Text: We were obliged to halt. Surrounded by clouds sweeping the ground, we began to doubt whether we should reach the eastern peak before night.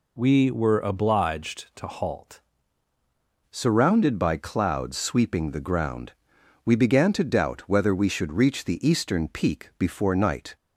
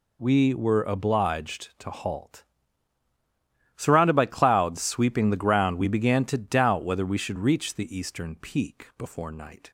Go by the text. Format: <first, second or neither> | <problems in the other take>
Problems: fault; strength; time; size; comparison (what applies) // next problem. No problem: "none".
second | changes voice at "Surrounded"; from 3.4 s on; 7.1 s long